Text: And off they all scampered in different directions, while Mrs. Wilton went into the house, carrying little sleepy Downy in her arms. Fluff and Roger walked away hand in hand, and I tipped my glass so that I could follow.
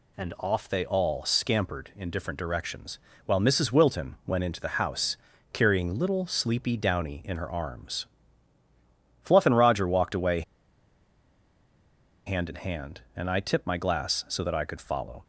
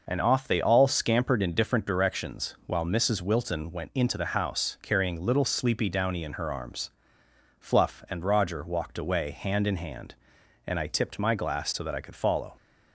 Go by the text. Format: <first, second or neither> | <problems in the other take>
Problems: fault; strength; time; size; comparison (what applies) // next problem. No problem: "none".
second | pauses between "away" and "hand"; strong; at 10.4 s; 1.8 s long